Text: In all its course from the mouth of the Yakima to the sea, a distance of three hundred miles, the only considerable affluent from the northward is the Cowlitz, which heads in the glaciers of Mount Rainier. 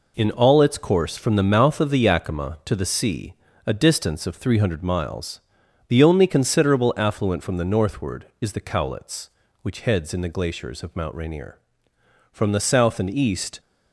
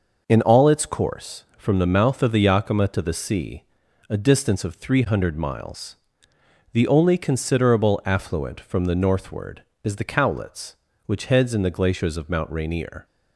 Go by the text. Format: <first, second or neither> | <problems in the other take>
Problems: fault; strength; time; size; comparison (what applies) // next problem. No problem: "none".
second | goes on to say "From the south and east"; noticeable; from 12.2 s on; 1.3 s long